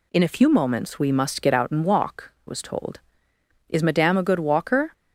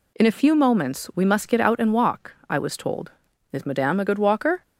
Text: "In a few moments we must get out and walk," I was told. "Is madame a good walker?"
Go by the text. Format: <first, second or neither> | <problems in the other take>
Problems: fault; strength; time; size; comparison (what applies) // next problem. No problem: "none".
second | skips "I"; at 2.3 s